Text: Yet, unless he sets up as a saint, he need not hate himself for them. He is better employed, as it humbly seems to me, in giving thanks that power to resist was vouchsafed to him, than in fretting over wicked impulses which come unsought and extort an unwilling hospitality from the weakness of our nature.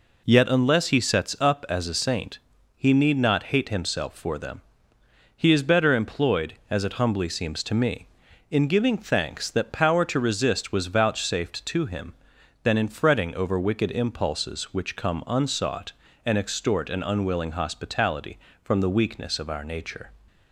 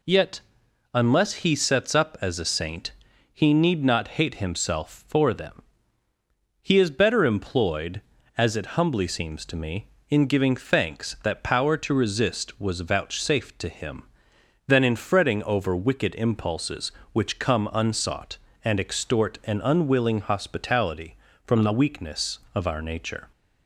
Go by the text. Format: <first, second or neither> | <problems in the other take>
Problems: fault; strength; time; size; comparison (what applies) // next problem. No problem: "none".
neither | none